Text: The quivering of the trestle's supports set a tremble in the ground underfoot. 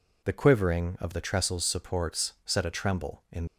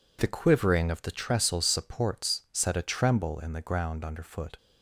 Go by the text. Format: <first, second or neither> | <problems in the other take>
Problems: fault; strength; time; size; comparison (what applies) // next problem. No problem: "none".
second | stops before "the ground underfoot"; at 3.4 s